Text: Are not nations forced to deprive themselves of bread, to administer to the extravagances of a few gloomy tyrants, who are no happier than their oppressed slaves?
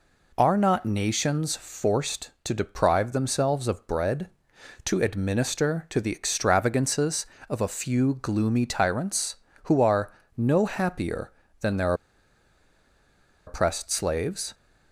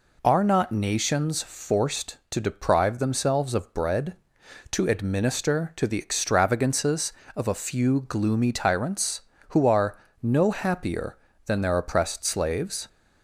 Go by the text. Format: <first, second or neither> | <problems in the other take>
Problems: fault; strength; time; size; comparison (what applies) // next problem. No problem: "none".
second | pauses between "are" and "no"; slight; at 10.1 s; 0.24 s long; slight in the second // pauses between "their" and "oppressed"; strong; at 11.9 s; 1.5 s long